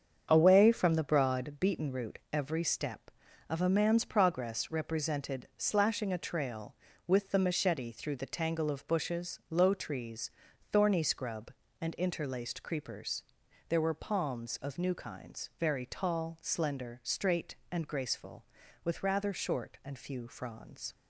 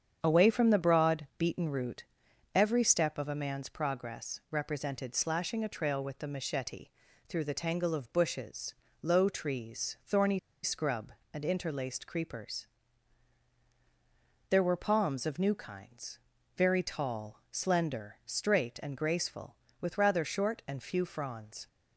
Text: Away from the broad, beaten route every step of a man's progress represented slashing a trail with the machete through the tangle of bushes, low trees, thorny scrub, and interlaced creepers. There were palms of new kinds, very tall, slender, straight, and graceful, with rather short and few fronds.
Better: first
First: starts louder than the rest; strong; until 1.3 s; 7.5 dB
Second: starts louder than the rest; strong; until 1.2 s; 8 dB // pauses between "route" and "every"; noticeable; at 2.0 s; 0.50 s long // pauses between "machete" and "through"; at 6.8 s; 0.38 s long // pauses between "thorny" and "scrub"; slight; at 10.3 s; 0.26 s long

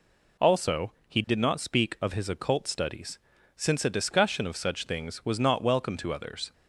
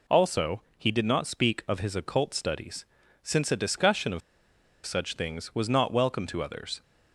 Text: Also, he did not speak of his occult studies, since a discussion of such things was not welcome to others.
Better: first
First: none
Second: pauses between "of" and "such"; noticeable; at 4.2 s; 0.65 s long

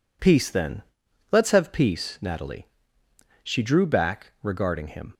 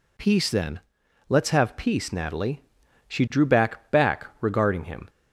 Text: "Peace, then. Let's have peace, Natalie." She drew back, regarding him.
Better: first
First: none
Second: says "back" twice; at 3.9 s

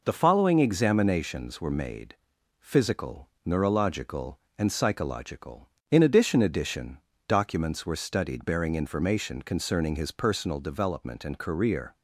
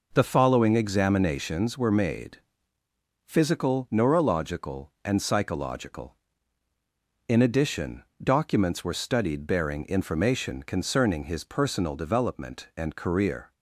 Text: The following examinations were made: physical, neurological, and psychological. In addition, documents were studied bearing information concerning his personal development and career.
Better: second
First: says "addition" twice; at 6.4 s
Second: none

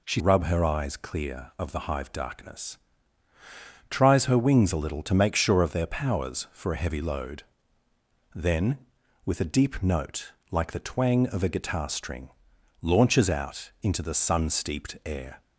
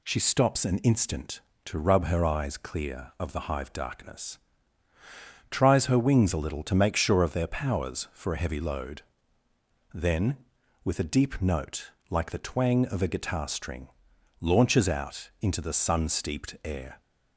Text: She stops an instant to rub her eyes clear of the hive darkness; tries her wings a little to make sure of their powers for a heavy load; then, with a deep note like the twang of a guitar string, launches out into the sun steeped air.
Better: second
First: skips "stops an instant to"; at 0.1 s // pauses between "note" and "like"; slight; at 10.3 s; 0.18 s long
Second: pauses between "note" and "like"; slight; at 11.9 s; 0.18 s long

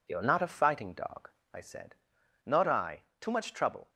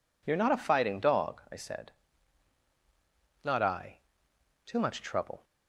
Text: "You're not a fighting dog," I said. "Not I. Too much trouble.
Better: neither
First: none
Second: none

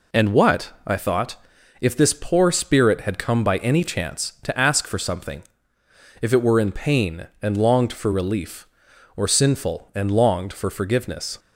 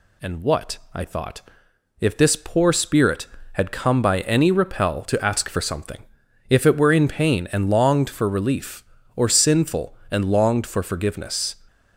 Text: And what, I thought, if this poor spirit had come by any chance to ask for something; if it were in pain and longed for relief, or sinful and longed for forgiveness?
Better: first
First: none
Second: says "repel" for "chance"; at 4.5 s

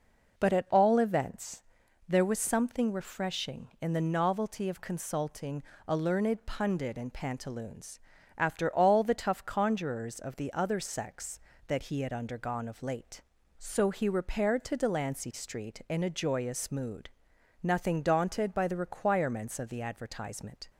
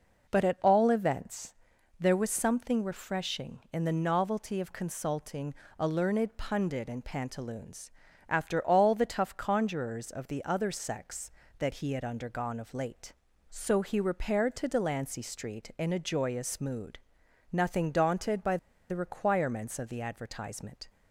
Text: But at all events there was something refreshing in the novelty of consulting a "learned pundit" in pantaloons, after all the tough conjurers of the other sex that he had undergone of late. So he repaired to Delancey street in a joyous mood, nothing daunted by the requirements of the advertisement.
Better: first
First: pauses between "events" and "there"; noticeable; at 1.6 s; 0.46 s long // pauses between "consulting" and "a"; slight; at 5.6 s; 0.26 s long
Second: pauses between "events" and "there"; noticeable; at 1.5 s; 0.46 s long // pauses between "consulting" and "a"; slight; at 5.5 s; 0.26 s long // pauses between "by" and "the"; slight; at 18.5 s; 0.32 s long

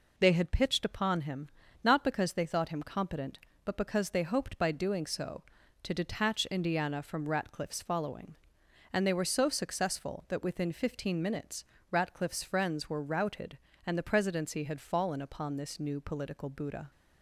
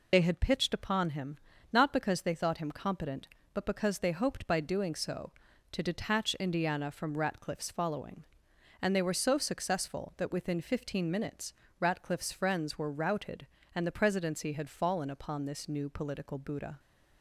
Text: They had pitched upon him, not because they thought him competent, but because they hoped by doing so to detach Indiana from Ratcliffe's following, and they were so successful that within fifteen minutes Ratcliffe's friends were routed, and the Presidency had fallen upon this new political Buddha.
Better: first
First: pauses between "minutes" and "Ratcliffe's"; slight; at 11.6 s; 0.26 s long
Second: loses the start of "They"; at 0.1 s; 60 ms // pauses between "minutes" and "Ratcliffe's"; slight; at 11.5 s; 0.26 s long

